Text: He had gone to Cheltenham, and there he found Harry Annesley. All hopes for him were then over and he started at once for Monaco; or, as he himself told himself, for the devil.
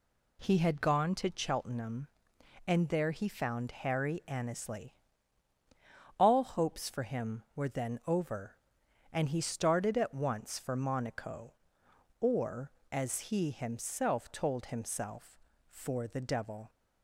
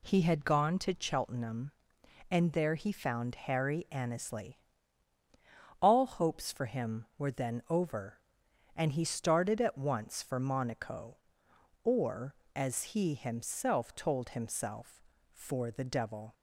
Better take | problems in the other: neither | none

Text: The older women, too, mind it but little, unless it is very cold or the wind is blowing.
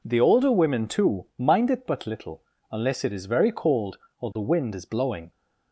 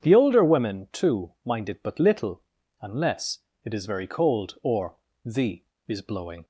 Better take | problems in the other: first | starts louder than the rest; strong; until 1.0 s; 8 dB // pauses between "unless" and "it"; slight; at 3.3 s; 0.26 s long // pauses between "or" and "the"; slight; at 4.9 s; 0.28 s long // skips "wind"; at 5.7 s

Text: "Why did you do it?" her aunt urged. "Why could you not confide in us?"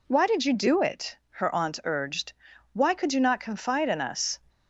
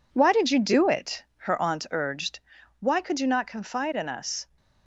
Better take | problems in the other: first | gets quieter; throughout; 6.5 dB

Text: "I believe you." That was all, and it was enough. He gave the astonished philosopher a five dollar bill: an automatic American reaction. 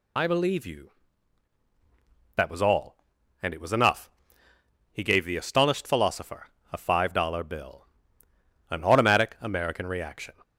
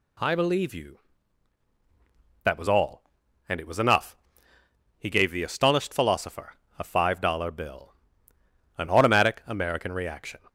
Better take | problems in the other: second | loses the start of "I"; at 0.1 s; 65 ms // pauses between "philosopher" and "a"; slight; at 6.4 s; 0.24 s long; slight in the second

